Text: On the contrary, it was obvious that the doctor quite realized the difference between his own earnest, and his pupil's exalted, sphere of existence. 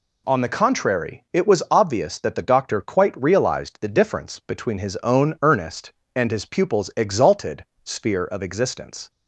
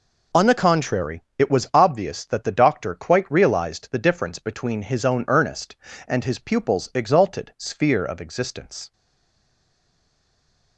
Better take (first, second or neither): first